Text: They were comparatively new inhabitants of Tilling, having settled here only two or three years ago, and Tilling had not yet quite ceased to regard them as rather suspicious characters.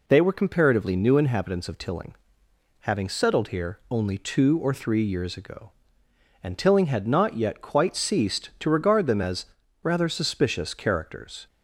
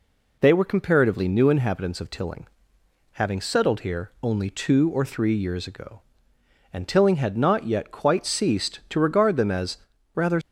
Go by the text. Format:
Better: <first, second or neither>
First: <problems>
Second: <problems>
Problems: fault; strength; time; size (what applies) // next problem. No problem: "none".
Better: first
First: pauses between "as" and "rather"; at 9.4 s; 0.38 s long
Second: pauses between "as" and "rather"; at 9.7 s; 0.38 s long // stops before "suspicious characters"; at 10.4 s